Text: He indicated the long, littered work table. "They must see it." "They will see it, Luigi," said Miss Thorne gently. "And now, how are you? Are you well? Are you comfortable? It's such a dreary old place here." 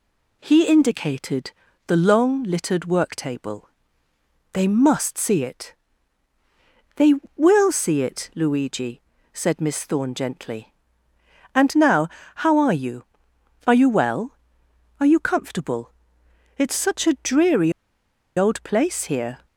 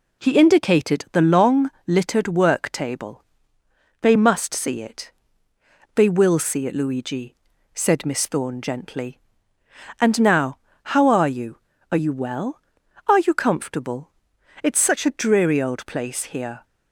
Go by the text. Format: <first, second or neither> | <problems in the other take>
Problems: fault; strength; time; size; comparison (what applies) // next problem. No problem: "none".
second | pauses between "indicated" and "the"; slight; at 1.5 s; 0.34 s long // pauses between "dreary" and "old"; noticeable; at 17.7 s; 0.66 s long